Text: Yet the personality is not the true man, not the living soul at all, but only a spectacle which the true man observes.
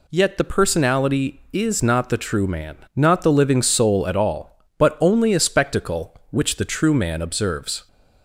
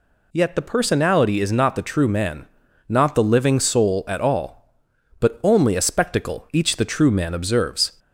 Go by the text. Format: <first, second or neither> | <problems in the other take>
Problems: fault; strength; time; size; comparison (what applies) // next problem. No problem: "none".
first | says "each" for "which"; at 6.5 s